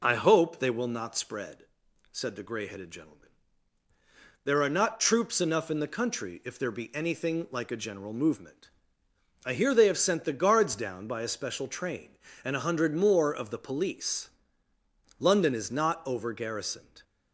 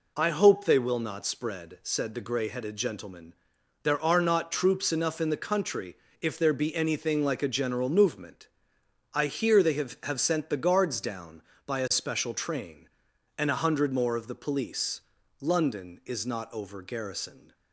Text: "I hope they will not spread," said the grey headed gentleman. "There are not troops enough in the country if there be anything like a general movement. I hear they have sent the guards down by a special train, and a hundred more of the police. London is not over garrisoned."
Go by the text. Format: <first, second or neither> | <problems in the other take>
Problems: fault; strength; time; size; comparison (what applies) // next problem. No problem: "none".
first | pauses between "country" and "if"; slight; at 5.9 s; 0.24 s long // says "have" twice; at 10.0 s